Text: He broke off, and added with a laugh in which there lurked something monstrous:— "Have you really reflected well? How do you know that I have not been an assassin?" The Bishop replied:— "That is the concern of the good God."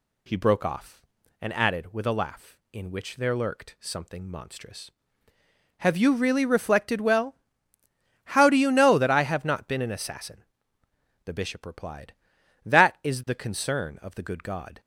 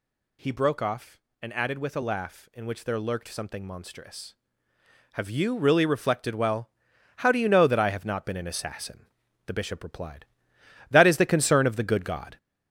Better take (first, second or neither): first